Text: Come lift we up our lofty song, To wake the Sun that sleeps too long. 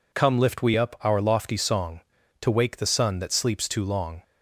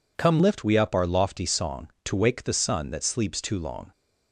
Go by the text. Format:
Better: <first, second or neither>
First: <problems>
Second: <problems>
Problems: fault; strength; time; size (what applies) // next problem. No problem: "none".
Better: first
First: none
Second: changes voice at "lift"; from 0.4 s on; 3.5 s long